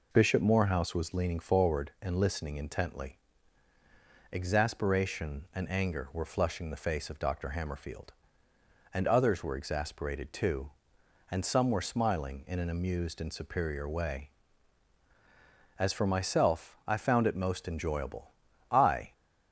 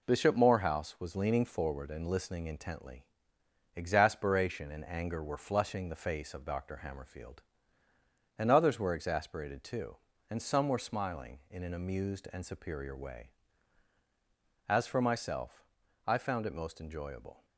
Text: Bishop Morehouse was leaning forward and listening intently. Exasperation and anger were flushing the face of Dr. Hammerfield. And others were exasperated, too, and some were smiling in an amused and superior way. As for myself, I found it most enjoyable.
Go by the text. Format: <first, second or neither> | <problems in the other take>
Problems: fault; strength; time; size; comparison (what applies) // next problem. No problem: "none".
second | goes on to say "I"; slight; from 18.6 s on; 0.42 s long